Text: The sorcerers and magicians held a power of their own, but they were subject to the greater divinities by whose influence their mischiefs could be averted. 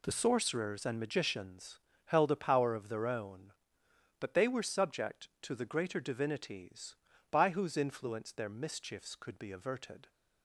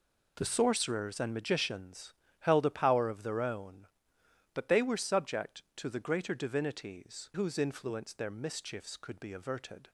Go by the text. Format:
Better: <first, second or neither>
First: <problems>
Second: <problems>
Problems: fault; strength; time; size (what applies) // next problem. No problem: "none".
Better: first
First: pauses between "magicians" and "held"; slight; at 1.8 s; 0.26 s long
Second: pauses between "magicians" and "held"; slight; at 2.1 s; 0.26 s long // skips "by"; at 7.3 s